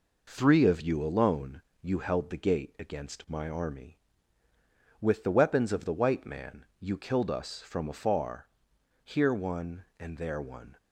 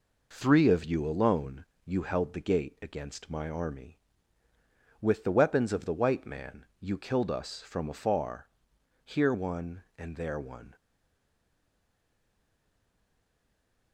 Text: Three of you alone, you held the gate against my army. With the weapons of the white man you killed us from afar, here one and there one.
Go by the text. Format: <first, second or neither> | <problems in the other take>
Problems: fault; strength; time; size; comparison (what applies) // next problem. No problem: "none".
first | stays silent after the last word; strong; from 10.7 s on; 3.2 s long